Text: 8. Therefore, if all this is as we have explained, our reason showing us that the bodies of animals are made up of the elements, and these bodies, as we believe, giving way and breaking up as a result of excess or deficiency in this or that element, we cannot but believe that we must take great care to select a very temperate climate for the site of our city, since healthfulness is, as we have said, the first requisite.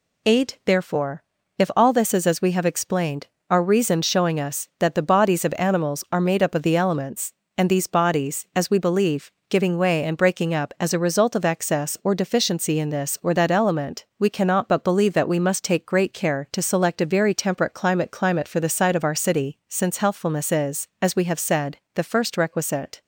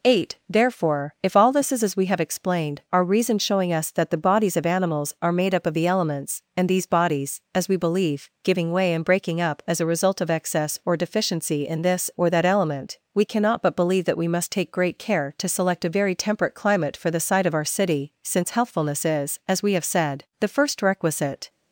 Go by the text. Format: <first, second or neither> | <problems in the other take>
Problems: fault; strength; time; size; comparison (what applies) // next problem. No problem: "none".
second | says "climate" twice; at 18.1 s